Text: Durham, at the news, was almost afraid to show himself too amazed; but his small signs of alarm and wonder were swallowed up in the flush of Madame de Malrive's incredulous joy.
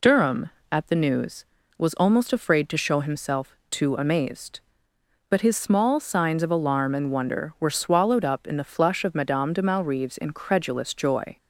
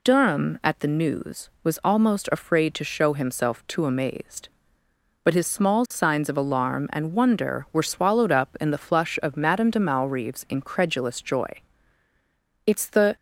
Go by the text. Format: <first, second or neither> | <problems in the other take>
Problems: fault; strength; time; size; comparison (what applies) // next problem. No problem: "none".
first | goes on to say "It's the"; from 12.6 s on; 0.50 s long